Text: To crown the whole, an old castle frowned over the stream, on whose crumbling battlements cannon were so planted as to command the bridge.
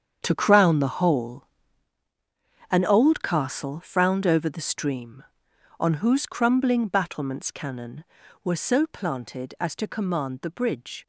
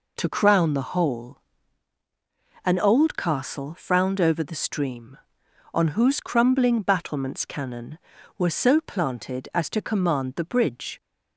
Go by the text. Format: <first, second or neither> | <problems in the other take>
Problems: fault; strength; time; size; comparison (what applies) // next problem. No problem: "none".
second | gets quieter; strong; throughout; 13 dB